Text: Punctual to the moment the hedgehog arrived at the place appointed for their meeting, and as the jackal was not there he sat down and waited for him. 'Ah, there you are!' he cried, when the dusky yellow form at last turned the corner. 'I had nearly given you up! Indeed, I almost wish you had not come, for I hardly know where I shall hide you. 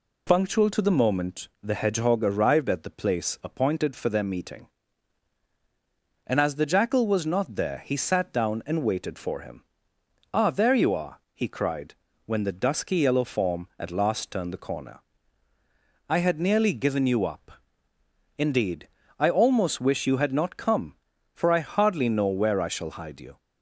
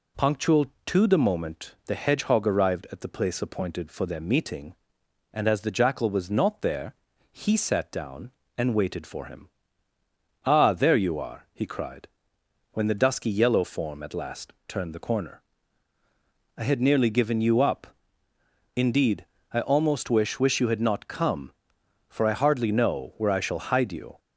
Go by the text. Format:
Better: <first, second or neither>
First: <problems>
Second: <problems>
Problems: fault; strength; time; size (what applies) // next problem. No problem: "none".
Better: first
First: none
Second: pauses between "there" and "he"; at 6.9 s; 0.38 s long // pauses between "last" and "turned"; slight; at 14.5 s; 0.16 s long // says "wish" twice; at 20.3 s